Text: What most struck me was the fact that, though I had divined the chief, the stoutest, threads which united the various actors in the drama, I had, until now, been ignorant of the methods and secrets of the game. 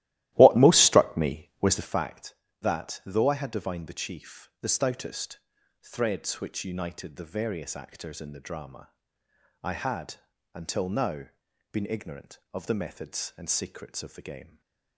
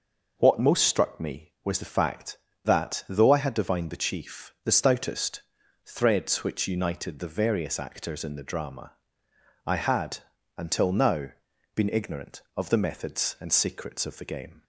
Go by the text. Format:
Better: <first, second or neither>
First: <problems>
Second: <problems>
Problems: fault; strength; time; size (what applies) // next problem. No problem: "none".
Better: second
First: starts louder than the rest; strong; until 2.0 s; 15 dB // stays silent after the last word; slight; from 14.4 s on; 0.5 s long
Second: none